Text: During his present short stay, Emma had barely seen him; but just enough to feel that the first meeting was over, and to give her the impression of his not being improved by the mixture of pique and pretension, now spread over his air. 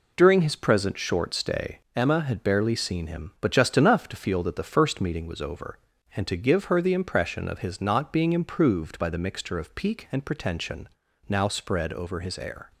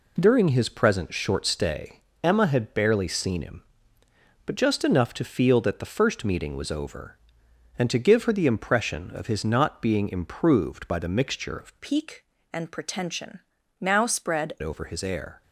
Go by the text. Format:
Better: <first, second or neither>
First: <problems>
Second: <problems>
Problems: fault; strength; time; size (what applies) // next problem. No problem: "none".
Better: first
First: none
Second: changes voice from "pique" to "spread"; from 11.8 to 14.5 s; 2.7 s long